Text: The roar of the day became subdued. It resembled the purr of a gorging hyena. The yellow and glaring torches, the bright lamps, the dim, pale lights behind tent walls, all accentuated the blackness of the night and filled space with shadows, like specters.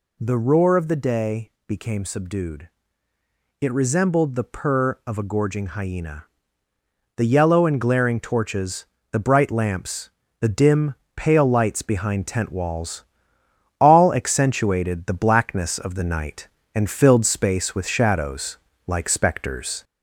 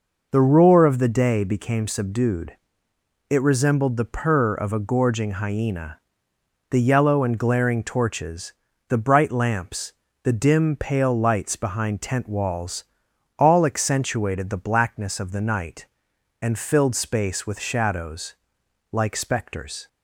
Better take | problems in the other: second | gets louder; slight; throughout; 2.5 dB // pauses between "day" and "became"; slight; at 1.5 s; 0.16 s long

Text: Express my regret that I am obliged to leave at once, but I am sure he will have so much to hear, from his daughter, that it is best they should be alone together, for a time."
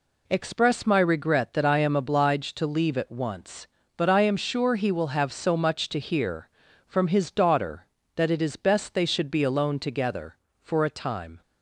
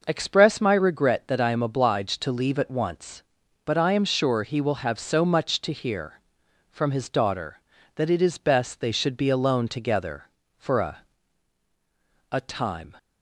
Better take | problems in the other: first | says "a" twice; at 12.3 s

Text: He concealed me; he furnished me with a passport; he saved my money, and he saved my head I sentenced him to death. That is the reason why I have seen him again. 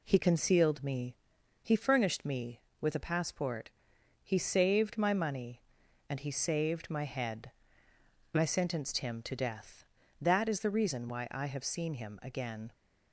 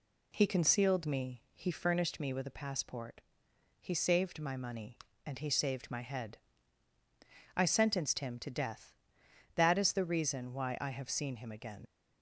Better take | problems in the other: first | pauses between "head" and "I"; at 6.3 s; 1.1 s long; noticeable in the first // leaves "again" unfinished; at 11.8 s; 65 ms

